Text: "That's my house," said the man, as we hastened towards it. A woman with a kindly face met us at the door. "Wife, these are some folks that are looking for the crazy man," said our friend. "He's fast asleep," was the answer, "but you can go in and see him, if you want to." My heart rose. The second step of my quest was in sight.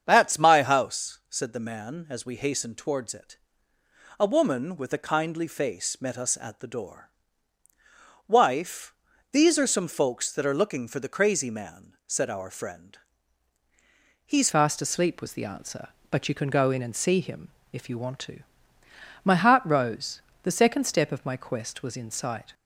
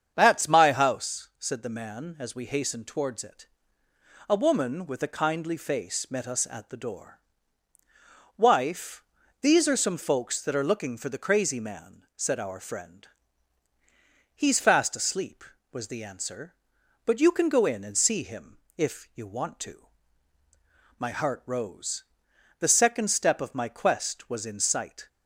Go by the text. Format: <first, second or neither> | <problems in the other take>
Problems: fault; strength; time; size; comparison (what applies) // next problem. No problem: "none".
second | starts louder than the rest; strong; until 1.0 s; 7.5 dB; strong in the second // changes voice at "fast"; from 14.5 s on; 8.0 s long